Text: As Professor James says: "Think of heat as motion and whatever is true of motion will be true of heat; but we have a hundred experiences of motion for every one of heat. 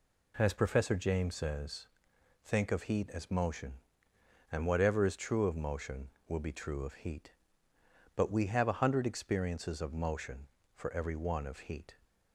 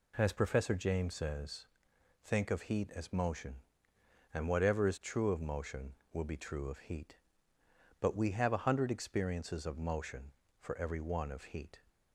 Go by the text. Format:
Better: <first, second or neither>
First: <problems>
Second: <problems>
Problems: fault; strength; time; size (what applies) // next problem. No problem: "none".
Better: neither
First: none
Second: none